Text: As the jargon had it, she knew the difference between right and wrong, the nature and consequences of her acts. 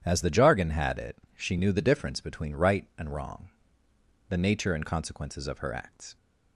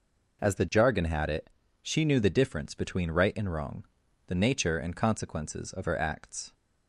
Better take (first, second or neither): neither